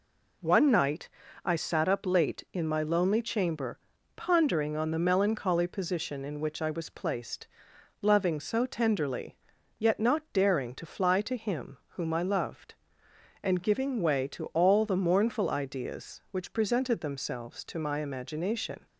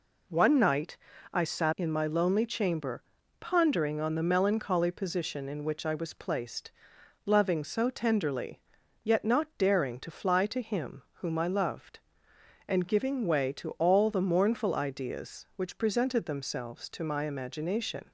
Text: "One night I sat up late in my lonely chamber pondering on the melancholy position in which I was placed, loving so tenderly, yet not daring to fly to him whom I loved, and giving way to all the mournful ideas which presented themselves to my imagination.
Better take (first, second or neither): first